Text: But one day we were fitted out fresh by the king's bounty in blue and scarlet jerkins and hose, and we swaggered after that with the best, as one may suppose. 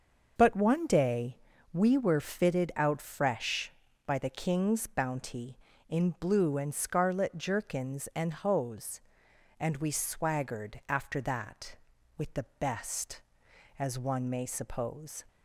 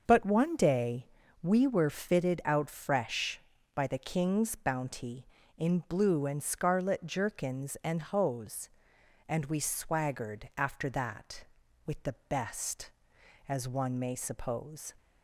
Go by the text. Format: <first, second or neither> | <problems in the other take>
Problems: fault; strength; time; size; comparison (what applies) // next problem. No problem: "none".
neither | starts louder than the rest; the same in both // pauses between "day" and "we"; slight; the same in both